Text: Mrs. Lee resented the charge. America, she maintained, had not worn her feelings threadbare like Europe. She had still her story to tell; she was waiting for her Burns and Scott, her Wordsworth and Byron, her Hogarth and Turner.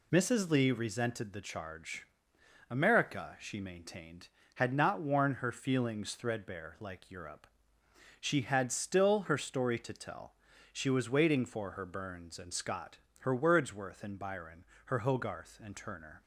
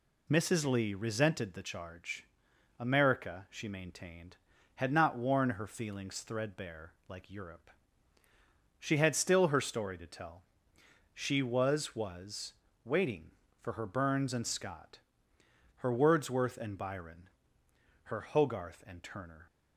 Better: first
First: none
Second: pauses between "threadbare" and "like"; slight; at 6.9 s; 0.16 s long // says "was" twice; at 11.9 s

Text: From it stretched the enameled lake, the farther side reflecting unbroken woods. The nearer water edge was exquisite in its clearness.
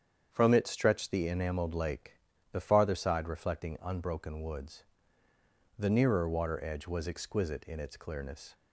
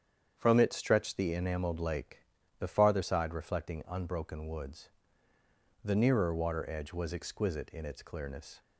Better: neither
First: starts louder than the rest; strong; until 1.3 s; 8 dB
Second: starts louder than the rest; strong; until 1.3 s; 8 dB

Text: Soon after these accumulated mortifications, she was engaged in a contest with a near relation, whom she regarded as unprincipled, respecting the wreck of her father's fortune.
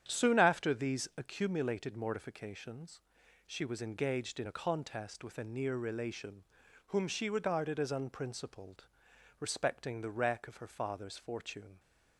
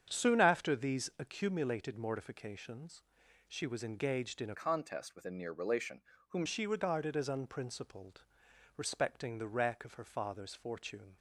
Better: first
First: starts louder than the rest; strong; until 1.0 s; 9.5 dB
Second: starts louder than the rest; strong; until 1.1 s; 8 dB // changes voice from "contest" to "whom"; from 4.5 to 6.4 s; 1.9 s long

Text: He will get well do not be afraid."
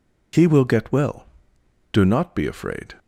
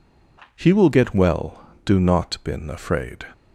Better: first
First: none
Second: says "been" for "be"; at 2.4 s

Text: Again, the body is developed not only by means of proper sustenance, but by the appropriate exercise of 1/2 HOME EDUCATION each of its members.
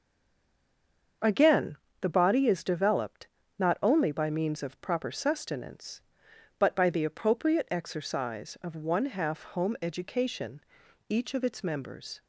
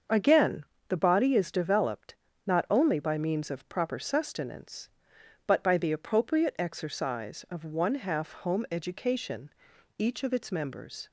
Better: second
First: stays silent before the first word; noticeable; until 1.2 s; 1.2 s long // starts louder than the rest; until 2.4 s; 6.5 dB // pauses between "developed" and "not"; slight; at 3.2 s; 0.30 s long // pauses between "EDUCATION" and "each"; noticeable; at 10.5 s; 0.50 s long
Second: starts louder than the rest; until 1.3 s; 6.5 dB // pauses between "developed" and "not"; slight; at 2.1 s; 0.30 s long // pauses between "EDUCATION" and "each"; noticeable; at 9.4 s; 0.50 s long

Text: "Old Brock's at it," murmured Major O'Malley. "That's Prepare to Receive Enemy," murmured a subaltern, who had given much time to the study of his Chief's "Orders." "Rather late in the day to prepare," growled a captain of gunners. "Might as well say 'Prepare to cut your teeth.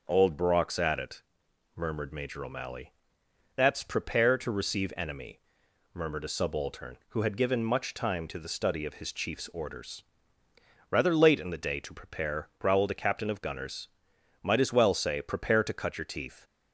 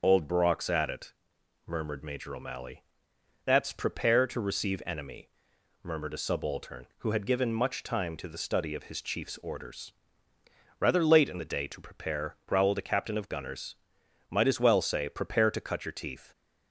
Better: first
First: none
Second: loses the start of "Old"; at 0.0 s; 55 ms // starts louder than the rest; until 1.0 s; 6.5 dB

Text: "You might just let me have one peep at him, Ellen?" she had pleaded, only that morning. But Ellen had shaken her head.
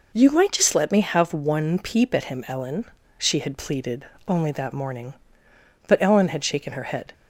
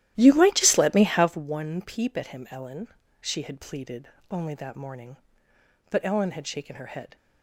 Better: first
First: none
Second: starts louder than the rest; strong; until 1.4 s; 13 dB

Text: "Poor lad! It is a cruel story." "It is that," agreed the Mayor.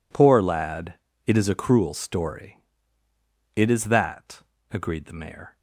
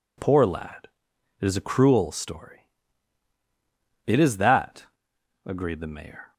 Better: neither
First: none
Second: none

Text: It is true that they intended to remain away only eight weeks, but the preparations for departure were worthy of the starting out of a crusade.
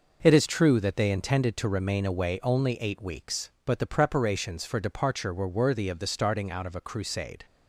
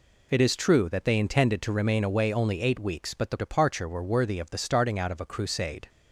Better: first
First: none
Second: skips "preparations for"; at 3.3 s

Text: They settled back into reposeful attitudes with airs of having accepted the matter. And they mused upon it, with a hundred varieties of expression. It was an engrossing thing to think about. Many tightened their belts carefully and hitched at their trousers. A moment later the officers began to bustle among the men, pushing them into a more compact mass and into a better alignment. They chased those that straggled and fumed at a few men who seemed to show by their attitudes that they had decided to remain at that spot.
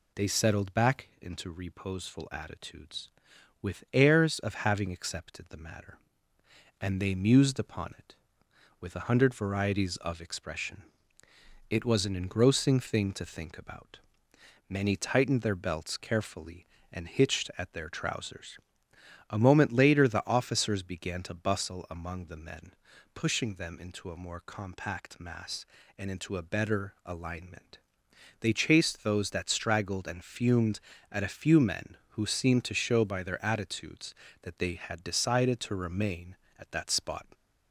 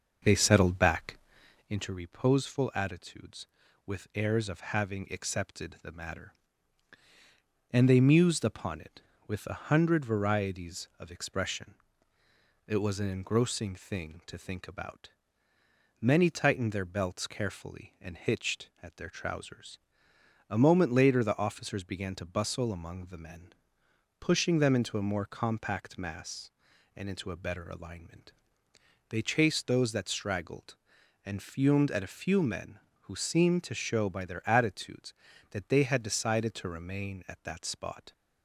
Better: first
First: none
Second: starts louder than the rest; until 1.8 s; 6.5 dB // pauses between "back" and "into"; noticeable; at 1.1 s; 0.52 s long

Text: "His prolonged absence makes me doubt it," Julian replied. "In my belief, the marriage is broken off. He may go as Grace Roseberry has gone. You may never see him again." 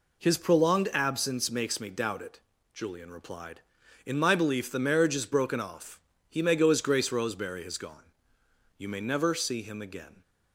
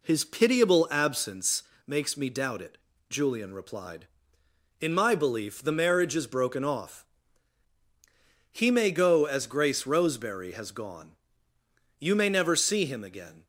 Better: first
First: none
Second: says "pitiable" for "prolonged"; at 0.2 s // pauses between "absence" and "makes"; slight; at 1.6 s; 0.24 s long

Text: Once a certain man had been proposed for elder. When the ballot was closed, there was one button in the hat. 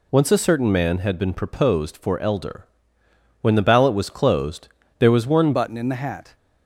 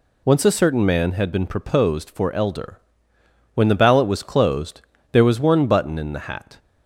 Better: second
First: changes voice at "button"; from 5.5 s on; 0.8 s long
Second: none

